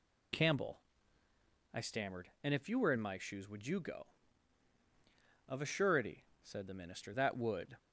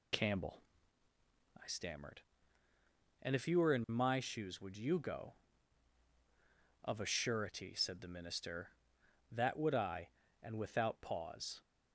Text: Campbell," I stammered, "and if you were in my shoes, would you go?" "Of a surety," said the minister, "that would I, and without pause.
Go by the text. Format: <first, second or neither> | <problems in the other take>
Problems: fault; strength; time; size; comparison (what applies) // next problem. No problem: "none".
second | stops before "I and without pause"; at 7.7 s